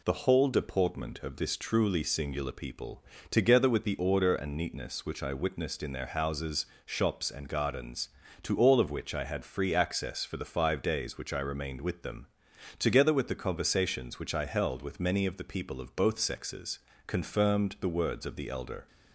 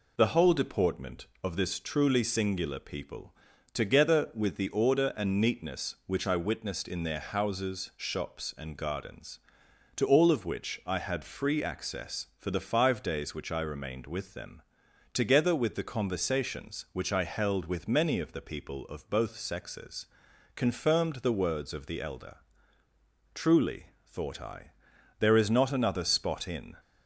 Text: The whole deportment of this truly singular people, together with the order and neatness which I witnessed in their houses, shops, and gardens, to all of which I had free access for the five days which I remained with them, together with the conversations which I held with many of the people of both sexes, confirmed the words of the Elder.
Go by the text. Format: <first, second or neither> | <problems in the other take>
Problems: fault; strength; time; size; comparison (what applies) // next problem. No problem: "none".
first | goes on to say "Truly thought I there is not another spot in"; strong; from 23.3 s on; 3.4 s long